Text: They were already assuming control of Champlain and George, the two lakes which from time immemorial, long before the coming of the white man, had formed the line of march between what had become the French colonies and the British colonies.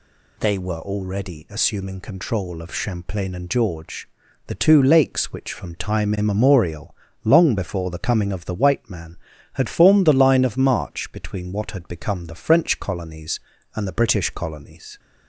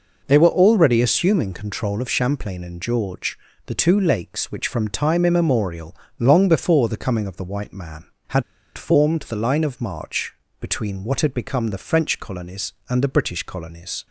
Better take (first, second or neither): first